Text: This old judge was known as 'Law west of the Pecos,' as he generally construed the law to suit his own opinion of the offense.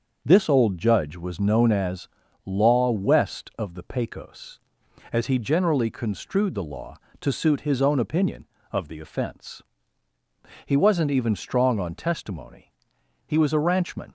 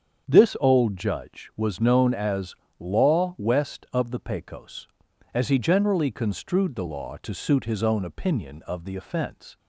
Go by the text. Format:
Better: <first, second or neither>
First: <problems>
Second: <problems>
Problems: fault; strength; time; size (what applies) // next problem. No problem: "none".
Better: second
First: starts louder than the rest; until 1.2 s; 6.5 dB // pauses between "as" and "Law"; slight; at 2.0 s; 0.36 s long // goes on to say "He wasn't even strong on testimony He was a ranchman"; strong; from 10.6 s on; 3.4 s long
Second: starts louder than the rest; strong; until 1.2 s; 7.5 dB // pauses between "as" and "Law"; slight; at 2.5 s; 0.24 s long